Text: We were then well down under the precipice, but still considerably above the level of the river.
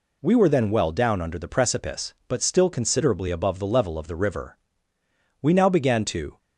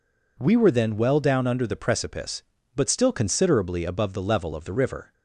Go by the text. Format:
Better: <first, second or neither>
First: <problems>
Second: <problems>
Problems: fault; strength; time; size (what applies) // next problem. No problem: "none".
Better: second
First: goes on to say "We now began to"; noticeable; from 5.4 s on; 0.96 s long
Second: none